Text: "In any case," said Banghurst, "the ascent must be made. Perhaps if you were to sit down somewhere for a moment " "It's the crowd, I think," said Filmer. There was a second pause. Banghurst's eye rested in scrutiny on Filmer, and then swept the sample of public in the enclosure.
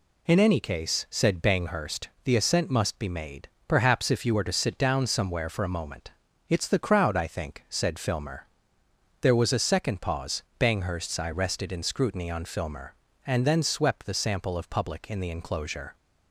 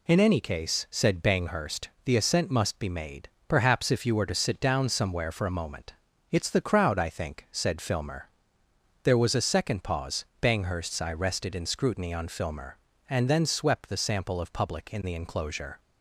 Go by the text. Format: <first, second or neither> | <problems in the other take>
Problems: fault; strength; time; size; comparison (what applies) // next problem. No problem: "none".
neither | none